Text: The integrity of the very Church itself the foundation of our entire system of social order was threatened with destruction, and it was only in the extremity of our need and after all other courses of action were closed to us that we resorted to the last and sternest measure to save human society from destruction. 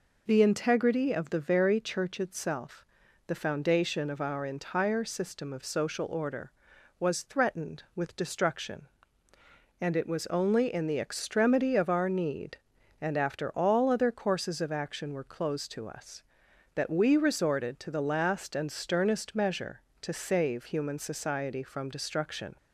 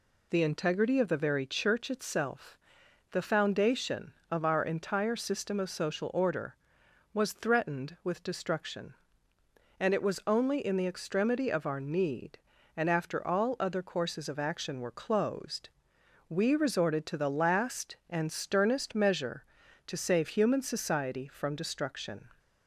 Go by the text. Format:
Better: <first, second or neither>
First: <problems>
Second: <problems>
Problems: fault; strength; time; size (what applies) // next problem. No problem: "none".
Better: first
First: pauses between "itself" and "the"; at 2.8 s; 0.44 s long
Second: pauses between "itself" and "the"; noticeable; at 2.5 s; 0.54 s long // skips "to us that"; at 15.9 s